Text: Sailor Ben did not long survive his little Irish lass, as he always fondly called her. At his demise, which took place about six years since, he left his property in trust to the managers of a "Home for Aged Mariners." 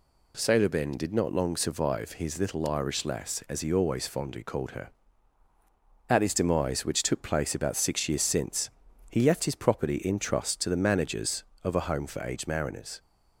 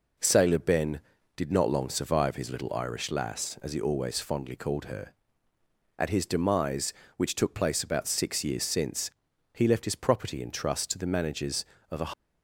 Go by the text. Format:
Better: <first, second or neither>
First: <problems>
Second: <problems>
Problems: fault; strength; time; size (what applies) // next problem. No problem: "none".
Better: first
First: none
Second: stops before "Home for Aged Mariners"; at 12.1 s